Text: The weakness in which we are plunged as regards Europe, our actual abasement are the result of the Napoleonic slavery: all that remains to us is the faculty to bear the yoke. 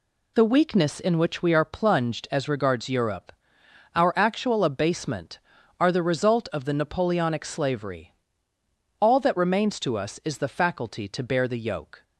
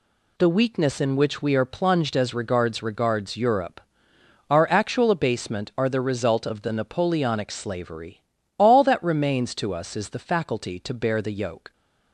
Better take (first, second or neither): first